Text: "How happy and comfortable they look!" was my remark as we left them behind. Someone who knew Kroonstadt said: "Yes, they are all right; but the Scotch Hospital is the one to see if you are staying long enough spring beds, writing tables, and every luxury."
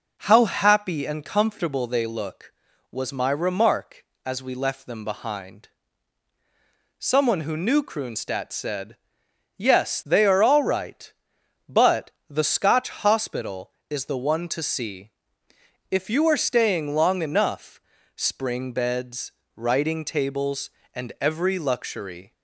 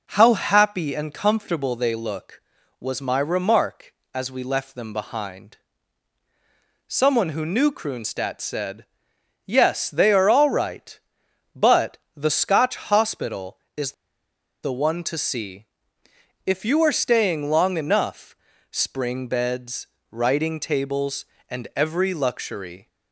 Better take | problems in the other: first | pauses between "but" and "the"; slight; at 11.9 s; 0.22 s long; slight in the first // pauses between "is" and "the"; noticeable; at 13.9 s; 0.71 s long // pauses between "see" and "if"; noticeable; at 15.6 s; 0.80 s long; noticeable in the first // pauses between "enough" and "spring"; slight; at 18.3 s; 0.36 s long; slight in the first

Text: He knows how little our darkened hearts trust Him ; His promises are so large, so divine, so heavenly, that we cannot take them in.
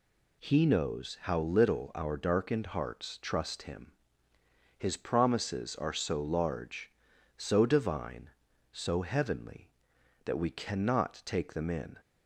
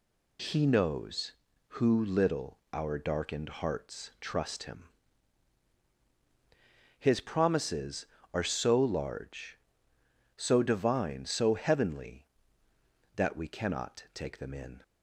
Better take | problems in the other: first | says "who" for "how"; at 1.7 s

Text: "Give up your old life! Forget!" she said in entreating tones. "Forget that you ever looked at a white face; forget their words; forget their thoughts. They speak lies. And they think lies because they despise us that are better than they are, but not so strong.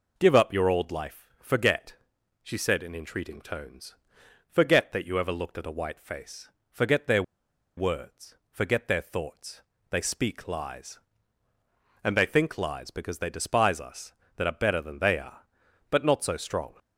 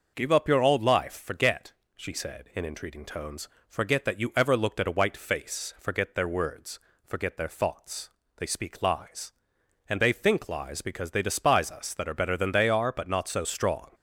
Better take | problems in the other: second | pauses between "their" and "words"; noticeable; at 7.2 s; 0.55 s long

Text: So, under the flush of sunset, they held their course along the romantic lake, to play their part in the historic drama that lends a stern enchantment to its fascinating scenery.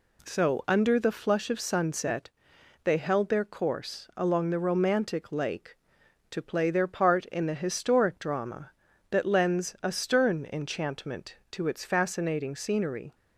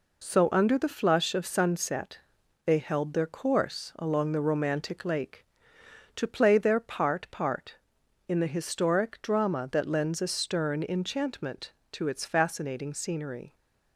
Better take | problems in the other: first | says "part" twice; at 7.3 s

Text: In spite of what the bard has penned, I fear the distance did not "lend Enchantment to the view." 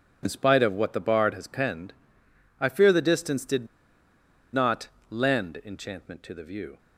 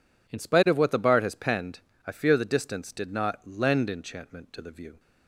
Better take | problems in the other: second | pauses between "did" and "not"; noticeable; at 3.6 s; 0.86 s long // pauses between "not" and "lend"; slight; at 4.8 s; 0.20 s long

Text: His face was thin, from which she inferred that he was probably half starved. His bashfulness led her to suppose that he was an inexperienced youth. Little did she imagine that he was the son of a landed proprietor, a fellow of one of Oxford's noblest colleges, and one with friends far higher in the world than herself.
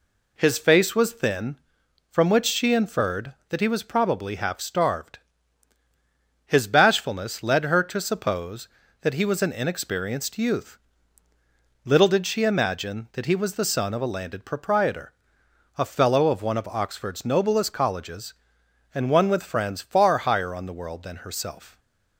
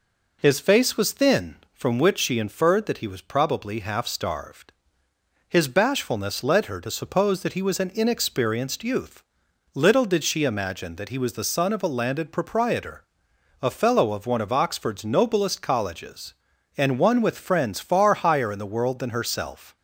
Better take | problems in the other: second | says "on" for "in"; at 20.5 s

